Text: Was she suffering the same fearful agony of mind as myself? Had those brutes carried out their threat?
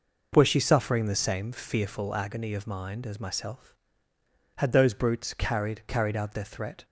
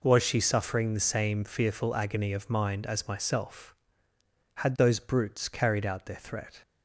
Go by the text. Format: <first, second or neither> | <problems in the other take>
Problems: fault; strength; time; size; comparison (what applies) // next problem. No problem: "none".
second | says "carried" twice; at 5.8 s